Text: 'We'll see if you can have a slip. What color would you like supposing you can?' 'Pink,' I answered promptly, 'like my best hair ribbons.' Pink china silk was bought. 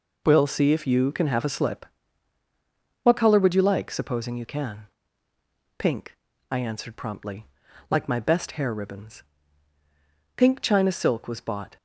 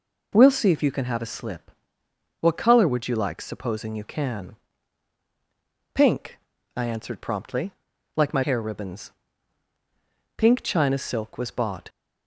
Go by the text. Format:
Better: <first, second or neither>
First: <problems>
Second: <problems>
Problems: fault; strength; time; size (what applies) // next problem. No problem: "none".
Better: first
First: none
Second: skips "best"; at 8.4 s